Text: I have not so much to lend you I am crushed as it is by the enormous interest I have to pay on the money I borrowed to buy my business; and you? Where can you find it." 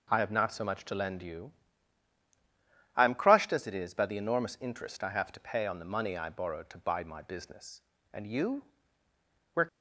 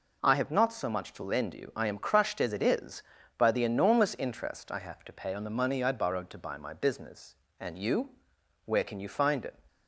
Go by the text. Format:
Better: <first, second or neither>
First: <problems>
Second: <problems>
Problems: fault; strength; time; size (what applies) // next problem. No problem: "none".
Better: second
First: pauses between "you" and "I"; strong; at 1.5 s; 1.4 s long // stops before "can you find it"; at 9.6 s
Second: none